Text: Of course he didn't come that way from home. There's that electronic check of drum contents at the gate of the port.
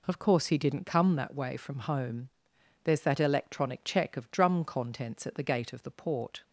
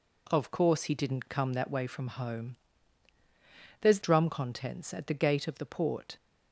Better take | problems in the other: first | skips "that electronic check of"; at 4.0 s

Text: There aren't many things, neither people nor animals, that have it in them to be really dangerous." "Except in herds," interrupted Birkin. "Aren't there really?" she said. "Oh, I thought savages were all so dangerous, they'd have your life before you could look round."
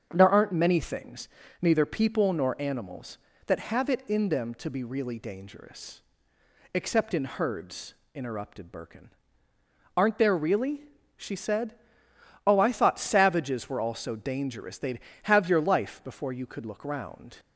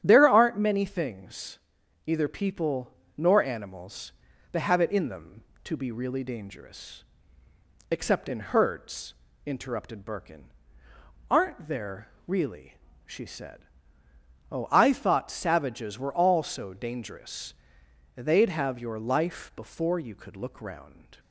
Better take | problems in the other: first | starts louder than the rest; strong; until 1.0 s; 9.5 dB; also in the first // says "either" for "neither"; at 2.0 s // pauses between "people" and "nor"; slight; at 2.9 s; 0.24 s long // pauses between "there" and "really"; slight; at 12.0 s; 0.18 s long

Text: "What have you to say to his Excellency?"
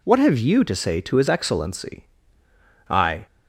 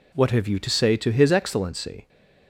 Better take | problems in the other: second | goes on to say "I"; slight; from 2.8 s on; 0.38 s long

